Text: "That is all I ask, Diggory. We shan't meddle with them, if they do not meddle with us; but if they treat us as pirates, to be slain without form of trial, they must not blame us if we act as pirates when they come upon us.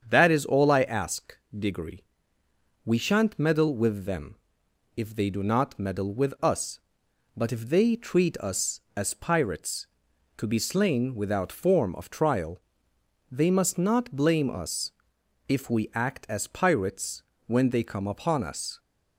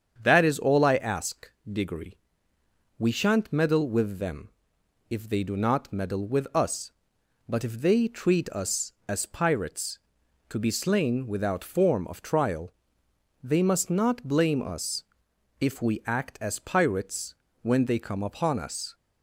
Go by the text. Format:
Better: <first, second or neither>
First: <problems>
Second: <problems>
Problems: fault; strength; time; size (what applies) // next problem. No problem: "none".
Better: neither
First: starts louder than the rest; strong; until 1.1 s; 7.5 dB // pauses between "us" and "if"; noticeable; at 14.9 s; 0.58 s long // pauses between "pirates" and "when"; slight; at 17.2 s; 0.24 s long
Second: starts louder than the rest; strong; until 1.2 s; 7.5 dB // pauses between "us" and "if"; noticeable; at 15.0 s; 0.58 s long // pauses between "pirates" and "when"; slight; at 17.3 s; 0.27 s long